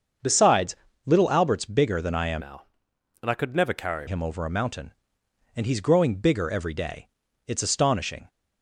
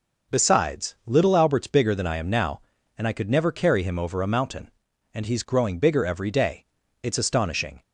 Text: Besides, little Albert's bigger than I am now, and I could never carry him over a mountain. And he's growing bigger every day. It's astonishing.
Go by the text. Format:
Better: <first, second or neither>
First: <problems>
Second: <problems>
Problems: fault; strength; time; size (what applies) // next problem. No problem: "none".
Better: second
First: starts louder than the rest; until 1.5 s; 7 dB // changes voice from "now" to "carry"; from 2.4 to 4.0 s; 1.6 s long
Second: none